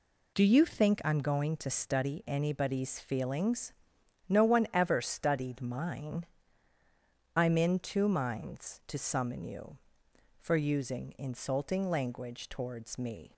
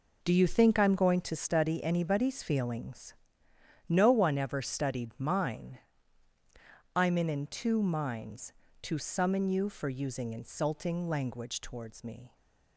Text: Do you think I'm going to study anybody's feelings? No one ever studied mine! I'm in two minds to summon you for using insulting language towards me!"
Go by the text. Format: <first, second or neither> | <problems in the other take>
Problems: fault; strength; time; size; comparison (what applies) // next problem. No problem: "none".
first | says "in" twice; at 7.2 s